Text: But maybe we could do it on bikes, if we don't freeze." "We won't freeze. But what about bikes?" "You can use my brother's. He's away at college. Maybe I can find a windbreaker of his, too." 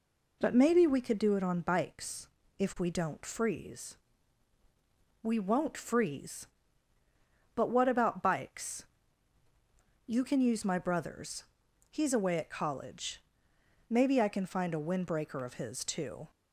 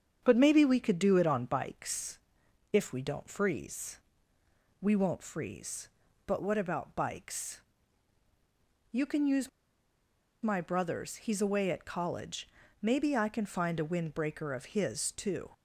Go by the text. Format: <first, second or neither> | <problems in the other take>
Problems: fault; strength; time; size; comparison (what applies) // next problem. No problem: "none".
first | starts louder than the rest; strong; until 1.2 s; 7.5 dB // pauses between "use" and "my"; noticeable; at 9.4 s; 0.93 s long